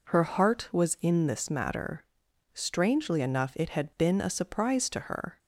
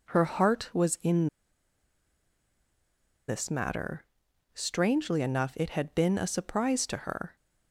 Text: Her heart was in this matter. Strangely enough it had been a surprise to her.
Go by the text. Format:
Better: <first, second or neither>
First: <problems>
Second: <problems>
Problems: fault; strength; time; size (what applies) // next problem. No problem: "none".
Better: first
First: none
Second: pauses between "in" and "this"; strong; at 1.2 s; 2.0 s long